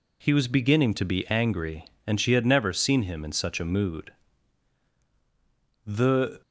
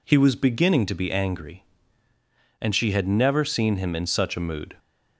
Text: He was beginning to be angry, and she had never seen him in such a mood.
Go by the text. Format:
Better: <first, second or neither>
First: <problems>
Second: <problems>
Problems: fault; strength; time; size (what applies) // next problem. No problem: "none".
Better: second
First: goes on to say "The"; from 5.8 s on; 0.58 s long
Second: none